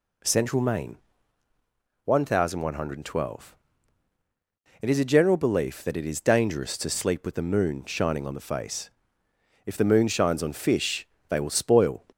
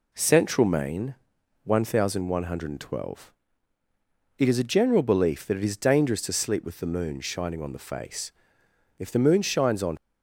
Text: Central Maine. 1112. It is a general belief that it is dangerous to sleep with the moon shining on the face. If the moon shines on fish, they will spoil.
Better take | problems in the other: first | stops before "fish they will spoil"; at 9.9 s

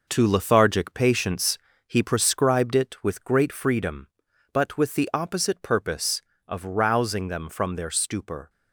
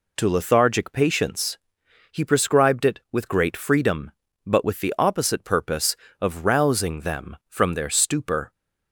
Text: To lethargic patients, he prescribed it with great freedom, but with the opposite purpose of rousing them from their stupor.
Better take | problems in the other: second | gets quieter; throughout; 7 dB

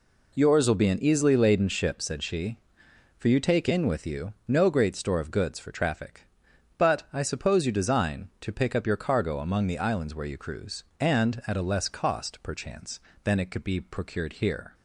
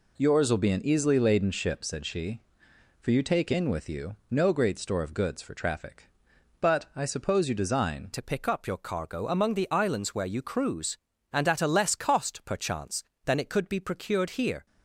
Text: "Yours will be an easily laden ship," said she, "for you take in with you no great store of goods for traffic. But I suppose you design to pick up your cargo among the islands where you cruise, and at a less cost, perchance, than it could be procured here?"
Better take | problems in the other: first | pauses between "you" and "no"; slight; at 4.1 s; 0.16 s long; slight in the first // changes voice at "to"; from 8.1 s on; 6.5 s long

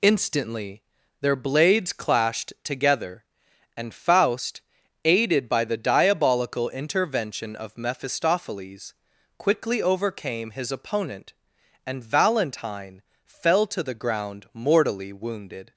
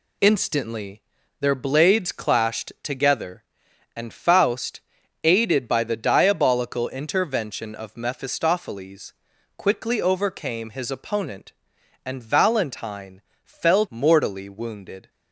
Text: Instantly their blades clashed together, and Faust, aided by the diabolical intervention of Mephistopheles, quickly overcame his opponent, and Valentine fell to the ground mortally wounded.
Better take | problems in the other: first | pauses between "Instantly" and "their"; at 1.0 s; 0.38 s long; also in the first // pauses between "Valentine" and "fell"; slight; at 13.2 s; 0.24 s long; slight in the first // skips "to the ground"; at 13.8 s

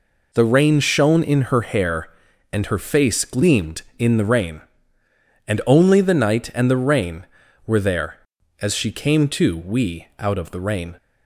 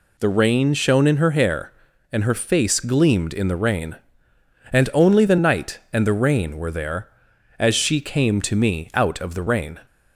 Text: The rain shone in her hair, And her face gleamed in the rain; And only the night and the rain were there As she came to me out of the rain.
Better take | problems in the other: second | says "we" for "me"; at 9.5 s

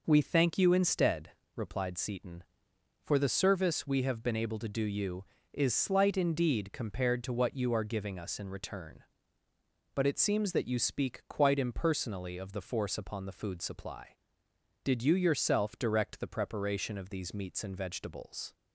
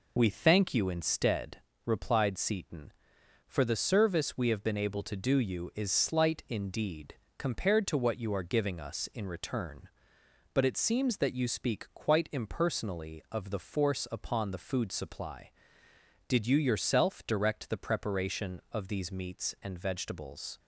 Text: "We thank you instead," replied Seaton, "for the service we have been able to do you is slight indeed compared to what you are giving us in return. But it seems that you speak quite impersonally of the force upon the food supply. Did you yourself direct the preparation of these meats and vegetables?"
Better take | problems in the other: first | loses the start of "We"; at 0.1 s; 25 ms // pauses between "indeed" and "compared"; slight; at 7.1 s; 0.22 s long

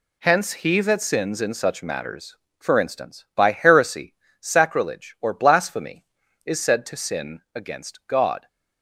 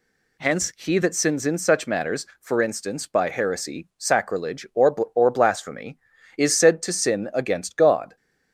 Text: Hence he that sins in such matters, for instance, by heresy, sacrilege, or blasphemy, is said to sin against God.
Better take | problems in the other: first | says "or" twice; at 5.1 s

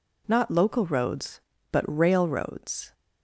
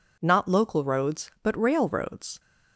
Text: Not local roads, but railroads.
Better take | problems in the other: neither | none

